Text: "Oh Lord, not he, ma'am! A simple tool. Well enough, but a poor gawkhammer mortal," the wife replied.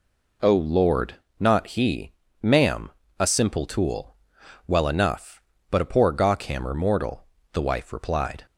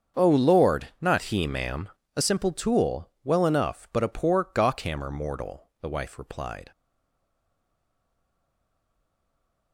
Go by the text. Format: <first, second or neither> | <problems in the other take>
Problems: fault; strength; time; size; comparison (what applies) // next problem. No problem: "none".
first | starts louder than the rest; strong; until 1.2 s; 7 dB // stays silent after the last word; strong; from 6.7 s on; 3.0 s long